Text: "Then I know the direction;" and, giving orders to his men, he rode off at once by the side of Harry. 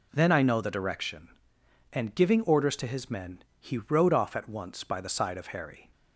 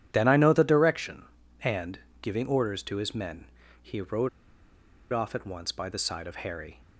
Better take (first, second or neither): first